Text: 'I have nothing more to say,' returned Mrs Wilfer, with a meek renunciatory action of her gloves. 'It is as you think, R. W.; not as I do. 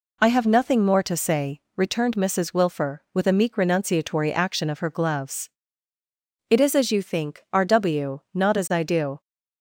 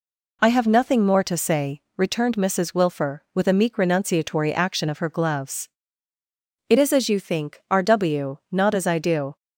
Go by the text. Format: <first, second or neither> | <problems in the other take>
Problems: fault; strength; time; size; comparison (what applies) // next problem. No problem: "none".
neither | none